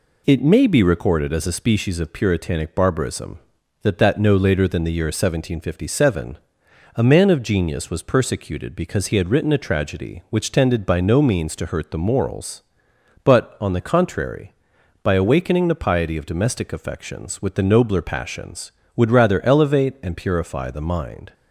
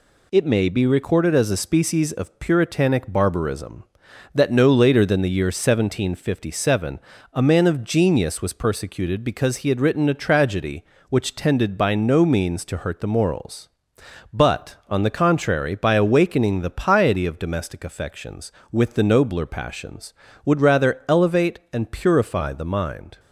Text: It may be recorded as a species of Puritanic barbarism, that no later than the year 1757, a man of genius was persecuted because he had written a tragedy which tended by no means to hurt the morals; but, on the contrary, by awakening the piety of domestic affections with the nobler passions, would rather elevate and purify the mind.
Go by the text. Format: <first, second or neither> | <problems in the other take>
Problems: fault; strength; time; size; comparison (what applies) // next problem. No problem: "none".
second | says "that" twice; at 3.9 s